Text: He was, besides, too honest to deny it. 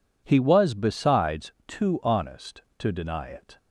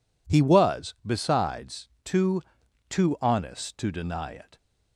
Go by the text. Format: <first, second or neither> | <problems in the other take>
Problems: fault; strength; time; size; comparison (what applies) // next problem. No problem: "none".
first | says "too" twice; at 2.8 s